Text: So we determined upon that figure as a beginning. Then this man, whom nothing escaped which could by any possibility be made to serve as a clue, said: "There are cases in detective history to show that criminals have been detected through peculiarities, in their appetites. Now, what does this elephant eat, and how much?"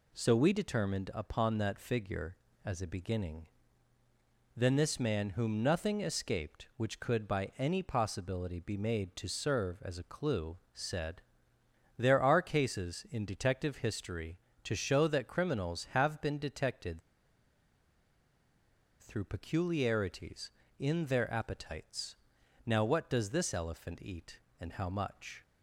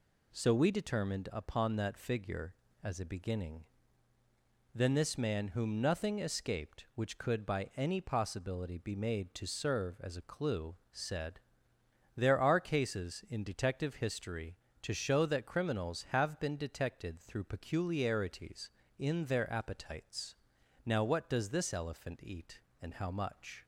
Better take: second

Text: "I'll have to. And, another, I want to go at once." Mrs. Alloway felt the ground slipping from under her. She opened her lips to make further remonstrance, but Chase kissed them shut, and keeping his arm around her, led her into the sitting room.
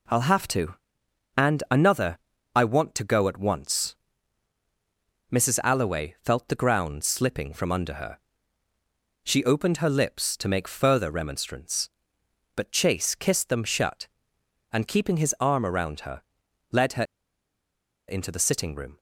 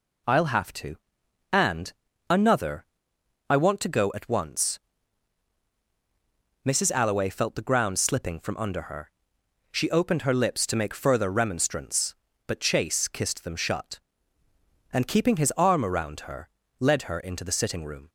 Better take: second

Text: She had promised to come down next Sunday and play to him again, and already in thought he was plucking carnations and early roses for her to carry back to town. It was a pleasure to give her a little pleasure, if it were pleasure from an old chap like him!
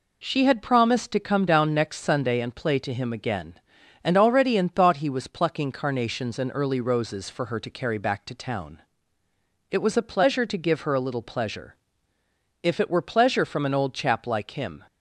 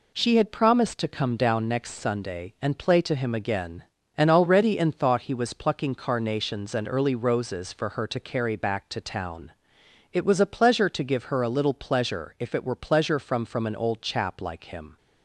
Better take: first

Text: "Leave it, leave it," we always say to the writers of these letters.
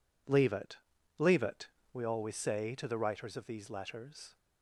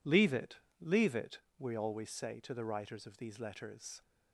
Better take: neither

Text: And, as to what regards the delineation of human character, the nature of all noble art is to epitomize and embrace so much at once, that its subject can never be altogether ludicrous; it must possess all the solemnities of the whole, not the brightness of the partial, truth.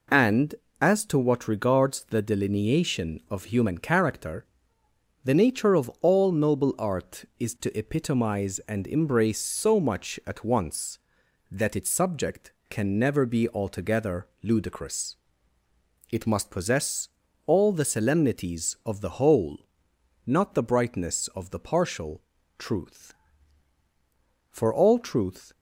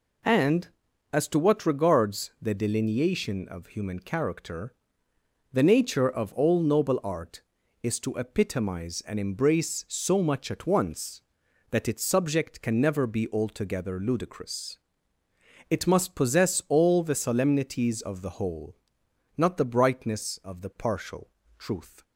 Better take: second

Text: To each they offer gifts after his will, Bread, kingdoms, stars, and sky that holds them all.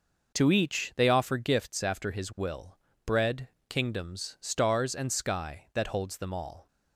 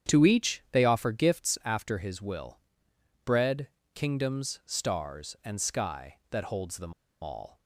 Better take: first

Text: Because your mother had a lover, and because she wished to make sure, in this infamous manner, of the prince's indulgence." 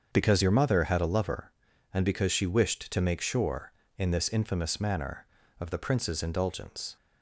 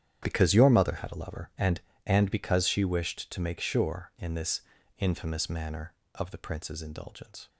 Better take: first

